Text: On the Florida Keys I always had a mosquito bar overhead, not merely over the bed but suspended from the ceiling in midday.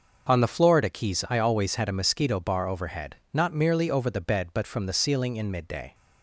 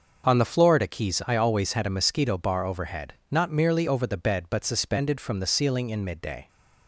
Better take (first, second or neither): second